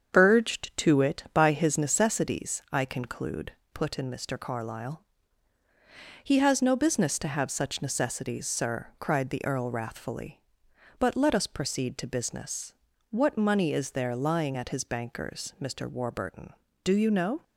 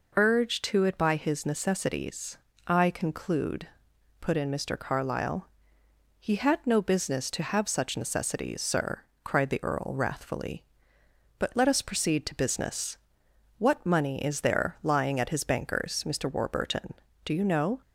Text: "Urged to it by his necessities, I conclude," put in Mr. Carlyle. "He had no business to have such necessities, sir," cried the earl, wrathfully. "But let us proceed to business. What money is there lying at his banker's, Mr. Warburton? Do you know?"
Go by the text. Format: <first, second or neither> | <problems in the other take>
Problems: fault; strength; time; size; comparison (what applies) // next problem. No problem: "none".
second | starts louder than the rest; strong; until 1.1 s; 7.5 dB // says "has" for "had"; at 6.3 s